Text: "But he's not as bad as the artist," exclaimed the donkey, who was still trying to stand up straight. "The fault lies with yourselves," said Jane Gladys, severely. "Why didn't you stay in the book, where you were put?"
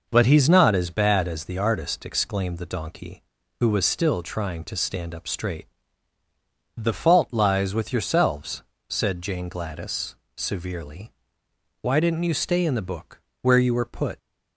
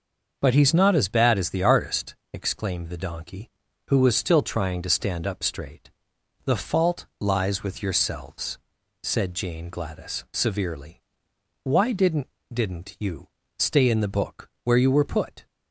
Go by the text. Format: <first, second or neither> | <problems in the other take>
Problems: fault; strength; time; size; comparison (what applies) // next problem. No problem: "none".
first | says "didn't" twice; at 12.5 s // pauses between "you" and "stay"; slight; at 13.2 s; 0.30 s long